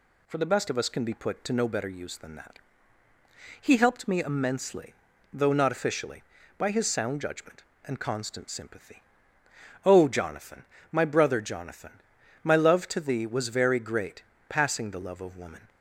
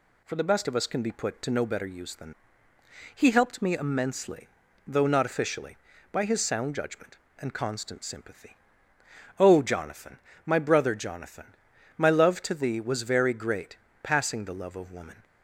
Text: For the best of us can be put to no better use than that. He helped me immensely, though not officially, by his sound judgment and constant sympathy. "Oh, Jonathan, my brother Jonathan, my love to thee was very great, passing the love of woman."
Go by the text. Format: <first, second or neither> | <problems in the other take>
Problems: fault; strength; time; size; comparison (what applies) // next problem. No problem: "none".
first | skips "that"; at 2.7 s